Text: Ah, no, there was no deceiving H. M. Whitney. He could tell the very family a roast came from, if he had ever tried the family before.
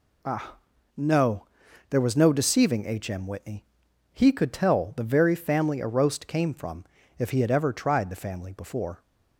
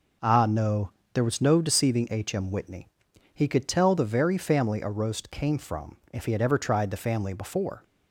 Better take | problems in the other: neither | none

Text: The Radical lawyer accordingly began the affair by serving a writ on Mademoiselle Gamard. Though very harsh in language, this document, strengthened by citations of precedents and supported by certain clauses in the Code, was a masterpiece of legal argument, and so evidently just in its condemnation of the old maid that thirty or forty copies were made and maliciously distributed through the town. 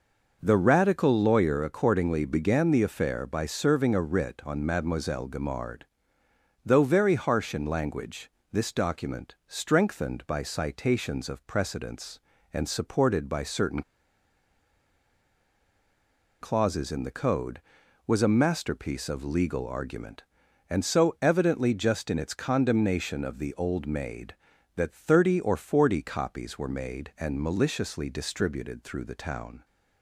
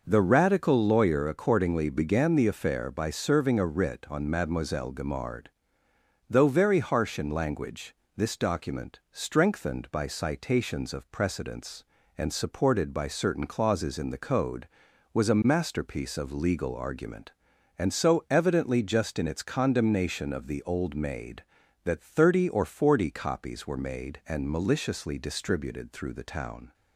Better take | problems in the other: second | pauses between "certain" and "clauses"; strong; at 13.8 s; 2.6 s long

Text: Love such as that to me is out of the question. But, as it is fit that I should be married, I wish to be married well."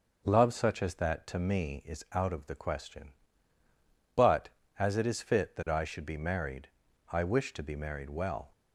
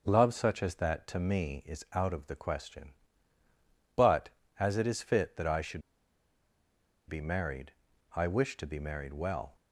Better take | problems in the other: first | pauses between "should" and "be"; strong; at 5.8 s; 1.2 s long

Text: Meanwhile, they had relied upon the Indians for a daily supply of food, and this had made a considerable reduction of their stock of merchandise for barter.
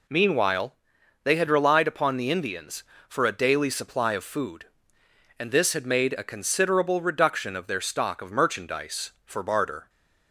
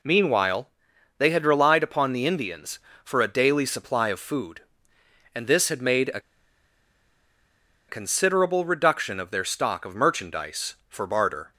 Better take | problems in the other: first | pauses between "a" and "considerable"; strong; at 6.1 s; 1.6 s long

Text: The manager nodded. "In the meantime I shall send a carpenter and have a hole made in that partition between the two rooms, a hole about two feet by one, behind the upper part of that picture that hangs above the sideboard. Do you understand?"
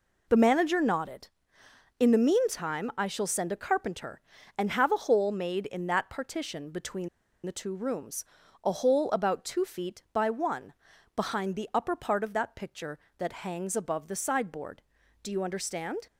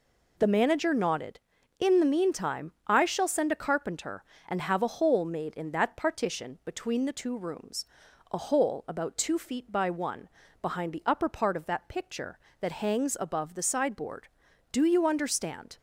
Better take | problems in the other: second | pauses between "between" and "the"; at 7.0 s; 0.37 s long

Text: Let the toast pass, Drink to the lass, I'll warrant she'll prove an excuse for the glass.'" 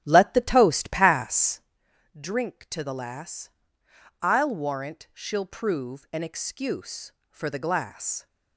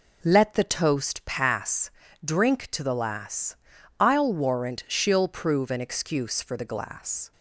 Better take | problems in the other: second | starts louder than the rest; strong; until 1.7 s; 12 dB

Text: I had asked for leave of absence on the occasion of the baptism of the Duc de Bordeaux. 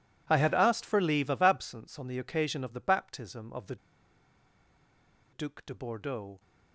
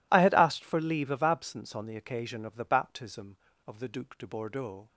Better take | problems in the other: second | pauses between "the" and "Duc"; strong; at 3.7 s; 1.5 s long

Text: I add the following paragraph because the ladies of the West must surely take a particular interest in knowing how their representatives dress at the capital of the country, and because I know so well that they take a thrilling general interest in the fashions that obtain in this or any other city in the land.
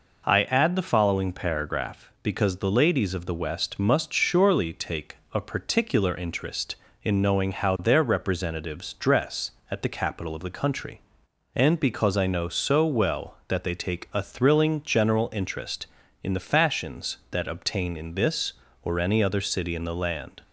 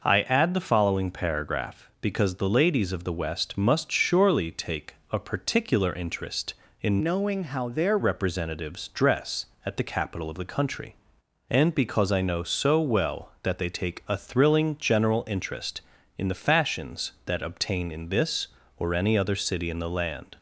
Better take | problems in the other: first | pauses between "take" and "a"; slight; at 4.9 s; 0.18 s long; slight in the first // changes voice from "knowing" to "their"; from 7.0 to 7.9 s; 0.9 s long

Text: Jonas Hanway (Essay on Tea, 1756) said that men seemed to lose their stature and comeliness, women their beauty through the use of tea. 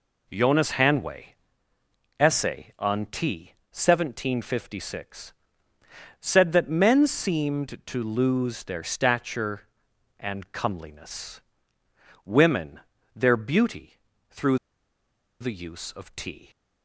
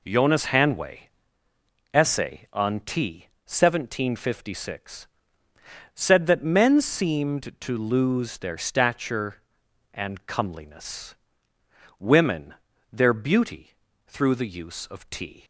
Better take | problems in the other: second | pauses between "women" and "their"; slight; at 12.7 s; 0.36 s long; also in the second // pauses between "beauty" and "through"; slight; at 13.9 s; 0.36 s long; slight in the second // pauses between "through" and "the"; noticeable; at 14.5 s; 0.82 s long

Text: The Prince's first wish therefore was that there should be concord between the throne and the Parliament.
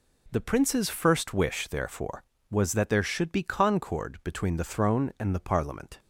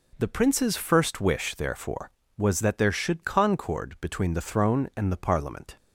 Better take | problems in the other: first | skips "be"; at 3.2 s

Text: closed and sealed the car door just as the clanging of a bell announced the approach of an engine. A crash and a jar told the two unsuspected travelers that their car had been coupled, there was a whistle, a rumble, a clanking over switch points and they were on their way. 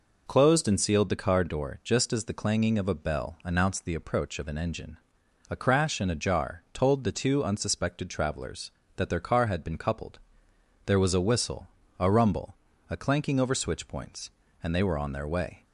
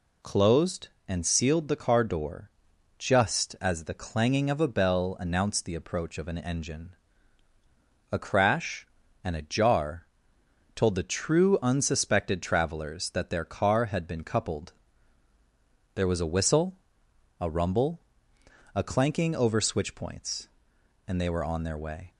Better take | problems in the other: first | pauses between "door" and "just"; noticeable; at 2.4 s; 0.50 s long // pauses between "jar" and "told"; noticeable; at 10.0 s; 0.70 s long // says "true" for "two"; at 11.0 s

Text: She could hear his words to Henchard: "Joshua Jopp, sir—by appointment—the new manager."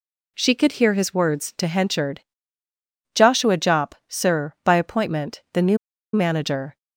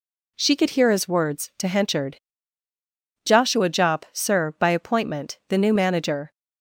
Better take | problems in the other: second | pauses between "new" and "manager"; at 5.7 s; 0.37 s long

